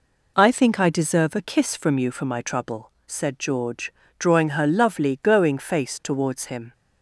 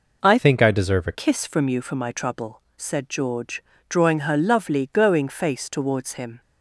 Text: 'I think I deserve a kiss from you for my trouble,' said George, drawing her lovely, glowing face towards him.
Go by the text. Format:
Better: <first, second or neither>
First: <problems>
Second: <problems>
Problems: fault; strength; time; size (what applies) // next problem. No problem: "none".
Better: first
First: none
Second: changes voice from "think" to "a"; from 0.3 to 1.1 s; 0.8 s long